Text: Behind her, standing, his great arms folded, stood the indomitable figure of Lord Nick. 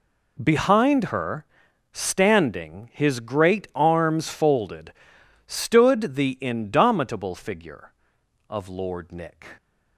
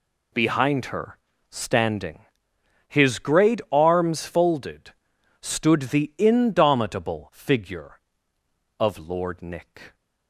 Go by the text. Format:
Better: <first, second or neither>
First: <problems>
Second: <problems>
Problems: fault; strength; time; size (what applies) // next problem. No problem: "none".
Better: neither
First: none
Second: none